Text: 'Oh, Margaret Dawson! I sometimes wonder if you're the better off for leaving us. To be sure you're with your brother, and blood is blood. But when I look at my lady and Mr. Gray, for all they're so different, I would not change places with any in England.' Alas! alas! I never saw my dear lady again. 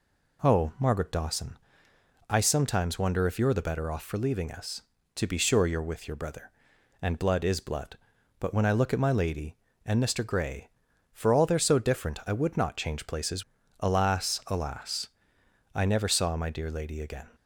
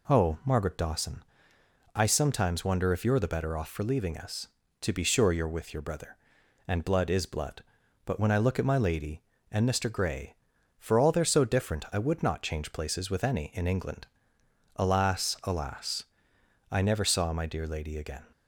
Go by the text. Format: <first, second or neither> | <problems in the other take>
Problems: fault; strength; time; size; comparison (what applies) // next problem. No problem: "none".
second | skips "with any in England"; at 13.6 s